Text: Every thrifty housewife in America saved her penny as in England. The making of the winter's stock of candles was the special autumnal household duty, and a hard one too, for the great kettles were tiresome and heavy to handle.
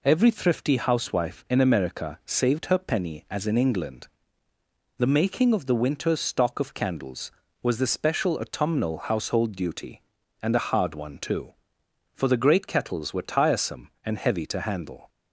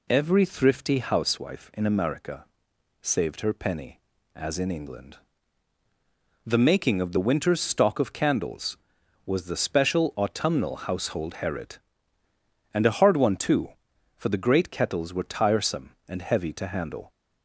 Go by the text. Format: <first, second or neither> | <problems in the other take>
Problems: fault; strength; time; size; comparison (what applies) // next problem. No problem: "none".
first | pauses between "America" and "saved"; noticeable; at 2.4 s; 0.56 s long // says "herit" for "duty"; at 11.4 s